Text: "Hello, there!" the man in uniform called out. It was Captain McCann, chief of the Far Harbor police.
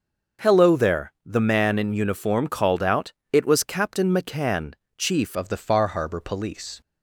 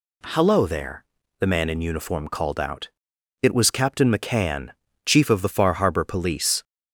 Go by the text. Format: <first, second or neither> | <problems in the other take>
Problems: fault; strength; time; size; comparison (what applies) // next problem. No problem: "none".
second | starts louder than the rest; noticeable; until 1.5 s; 6 dB // changes voice at "of"; from 5.3 s on; 1.5 s long